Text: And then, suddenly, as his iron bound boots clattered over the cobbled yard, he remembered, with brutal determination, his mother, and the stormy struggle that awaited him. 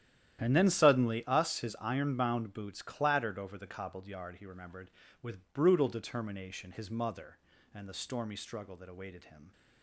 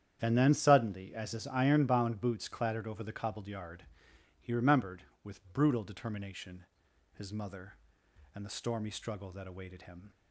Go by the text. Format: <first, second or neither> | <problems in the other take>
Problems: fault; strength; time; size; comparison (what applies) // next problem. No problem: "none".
second | starts louder than the rest; strong; until 1.4 s; 11.5 dB; strong in the second // says "us" for "as"; at 1.2 s